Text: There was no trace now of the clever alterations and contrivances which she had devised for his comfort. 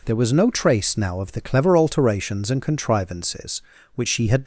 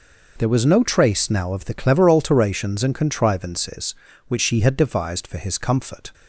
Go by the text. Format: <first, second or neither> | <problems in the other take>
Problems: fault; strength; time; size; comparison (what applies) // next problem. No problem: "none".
second | stops before "devised for his comfort"; at 4.4 s